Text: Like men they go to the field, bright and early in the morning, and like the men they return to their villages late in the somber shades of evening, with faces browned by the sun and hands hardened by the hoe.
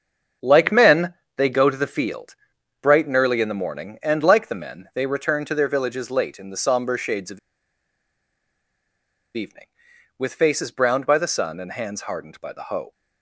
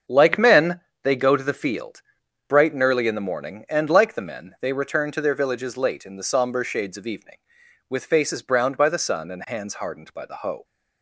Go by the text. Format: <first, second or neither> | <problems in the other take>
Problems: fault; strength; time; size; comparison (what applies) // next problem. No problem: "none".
second | starts louder than the rest; until 1.6 s; 7 dB; also in the second // pauses between "men" and "they"; slight; at 1.1 s; 0.22 s long; slight in the second // pauses between "of" and "evening"; strong; at 7.3 s; 1.9 s long